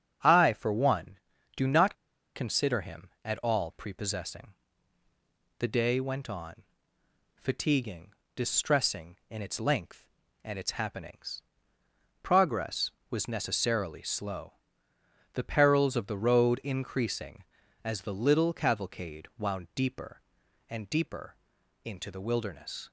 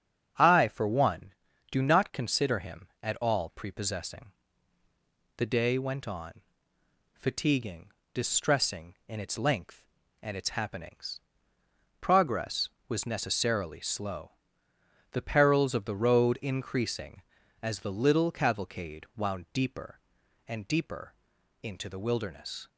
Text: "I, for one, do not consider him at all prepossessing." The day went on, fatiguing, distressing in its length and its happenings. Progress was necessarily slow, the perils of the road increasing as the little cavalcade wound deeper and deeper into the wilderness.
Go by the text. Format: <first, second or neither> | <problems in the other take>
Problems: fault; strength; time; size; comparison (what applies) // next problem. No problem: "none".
second | starts louder than the rest; strong; until 1.6 s; 7.5 dB; strong in the second // pauses between "not" and "consider"; at 1.9 s; 0.40 s long // pauses between "deeper" and "into"; noticeable; at 21.3 s; 0.50 s long; noticeable in the second